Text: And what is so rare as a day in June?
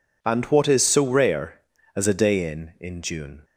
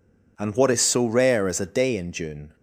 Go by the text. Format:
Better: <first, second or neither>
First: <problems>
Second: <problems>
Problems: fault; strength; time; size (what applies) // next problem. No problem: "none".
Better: second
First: says "in" twice; at 2.7 s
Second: none